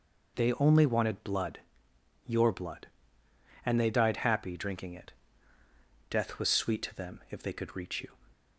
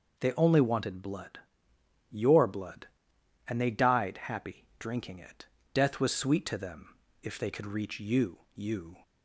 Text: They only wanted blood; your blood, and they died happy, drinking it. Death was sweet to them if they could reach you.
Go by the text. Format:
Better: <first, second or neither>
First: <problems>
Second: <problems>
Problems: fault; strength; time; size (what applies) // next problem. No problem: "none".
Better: first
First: none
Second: pauses between "them" and "if"; slight; at 6.9 s; 0.24 s long // says "you" twice; at 8.5 s